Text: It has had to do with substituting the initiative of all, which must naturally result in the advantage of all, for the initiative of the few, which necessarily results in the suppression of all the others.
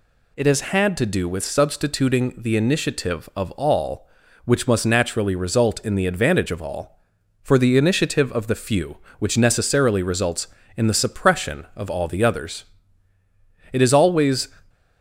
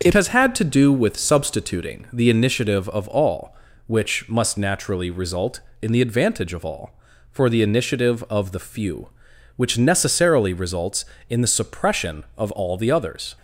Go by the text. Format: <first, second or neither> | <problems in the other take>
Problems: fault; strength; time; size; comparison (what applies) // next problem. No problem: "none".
second | goes on to say "It is always"; noticeable; from 13.7 s on; 0.76 s long